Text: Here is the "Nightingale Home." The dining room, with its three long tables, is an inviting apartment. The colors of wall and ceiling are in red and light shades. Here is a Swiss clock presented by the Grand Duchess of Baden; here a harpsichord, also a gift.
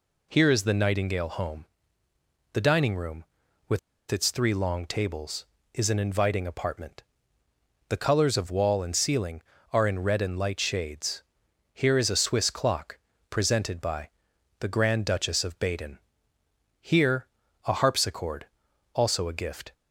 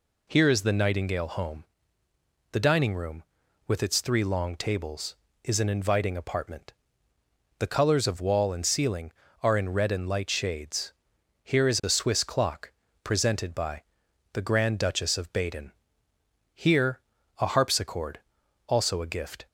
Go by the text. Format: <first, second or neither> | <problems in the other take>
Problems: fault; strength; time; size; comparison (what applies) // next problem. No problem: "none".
second | pauses between "with" and "its"; slight; at 3.7 s; 0.31 s long // pauses between "clock" and "presented"; slight; at 12.9 s; 0.32 s long; slight in the second // pauses between "by" and "the"; noticeable; at 14.0 s; 0.48 s long; noticeable in the second // pauses between "here" and "a"; at 17.2 s; 0.38 s long; also in the second